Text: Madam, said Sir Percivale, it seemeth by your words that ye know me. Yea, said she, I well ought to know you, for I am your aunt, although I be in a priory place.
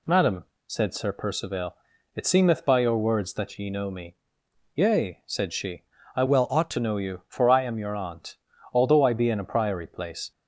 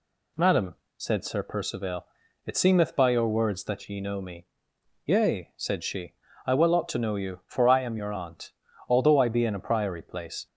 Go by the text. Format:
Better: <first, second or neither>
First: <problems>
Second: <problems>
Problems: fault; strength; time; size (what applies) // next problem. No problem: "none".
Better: second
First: changes voice from "well" to "to"; from 6.2 to 6.7 s; 0.5 s long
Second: none